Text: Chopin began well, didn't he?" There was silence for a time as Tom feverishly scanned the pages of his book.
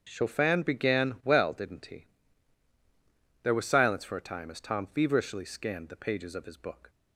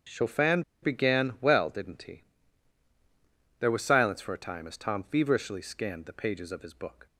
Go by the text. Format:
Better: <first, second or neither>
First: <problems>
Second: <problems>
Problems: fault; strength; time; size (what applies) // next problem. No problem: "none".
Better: first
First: starts louder than the rest; strong; until 1.0 s; 7.5 dB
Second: starts louder than the rest; strong; until 1.2 s; 7.5 dB // pauses between "Chopin" and "began"; slight; at 0.6 s; 0.20 s long